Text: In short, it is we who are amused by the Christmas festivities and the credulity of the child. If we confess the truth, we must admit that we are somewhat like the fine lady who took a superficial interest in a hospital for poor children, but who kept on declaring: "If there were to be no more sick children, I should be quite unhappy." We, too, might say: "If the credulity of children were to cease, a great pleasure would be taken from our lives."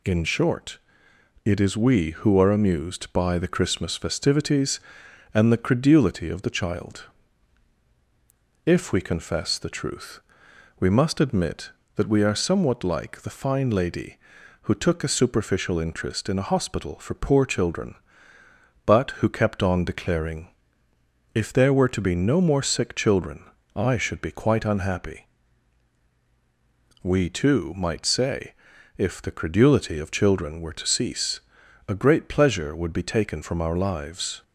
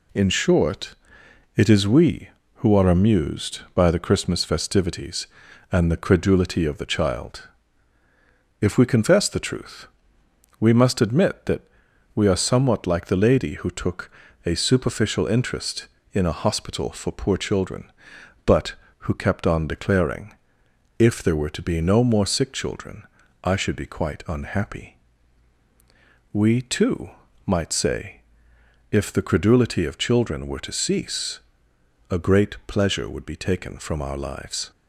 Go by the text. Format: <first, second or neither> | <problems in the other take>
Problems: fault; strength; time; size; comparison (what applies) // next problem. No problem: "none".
first | pauses between "that" and "we"; noticeable; at 11.6 s; 0.54 s long // skips "fine"; at 13.2 s // pauses between "took" and "a"; slight; at 14.1 s; 0.34 s long